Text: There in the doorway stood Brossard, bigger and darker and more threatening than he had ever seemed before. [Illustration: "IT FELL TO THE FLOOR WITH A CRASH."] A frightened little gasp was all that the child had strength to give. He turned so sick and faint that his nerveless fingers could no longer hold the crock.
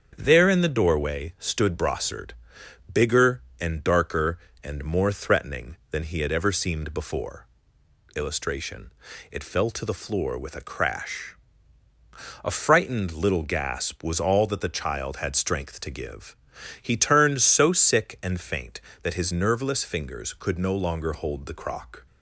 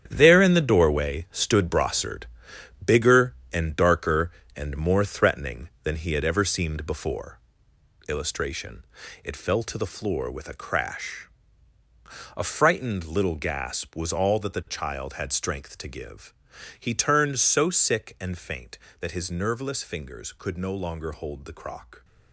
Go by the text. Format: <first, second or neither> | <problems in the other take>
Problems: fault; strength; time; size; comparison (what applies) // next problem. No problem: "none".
first | gets quieter; strong; throughout; 10.5 dB // starts louder than the rest; strong; until 1.0 s; 9 dB; strong in the first